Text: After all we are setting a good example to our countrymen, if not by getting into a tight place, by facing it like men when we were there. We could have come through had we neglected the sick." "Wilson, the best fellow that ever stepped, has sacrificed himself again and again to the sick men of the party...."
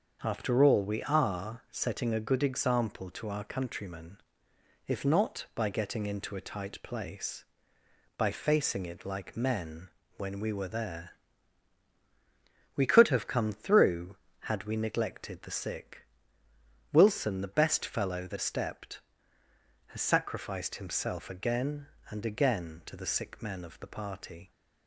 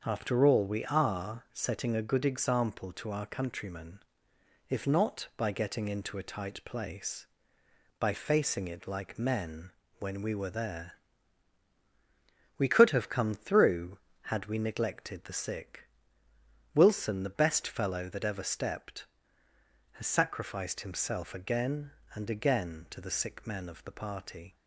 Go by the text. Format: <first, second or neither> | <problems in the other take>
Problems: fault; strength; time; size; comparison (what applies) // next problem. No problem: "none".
second | starts louder than the rest; until 1.2 s; 6.5 dB; also in the second // pauses between "men" and "when"; slight; at 9.8 s; 0.28 s long; slight in the second // skips "ever"; at 18.3 s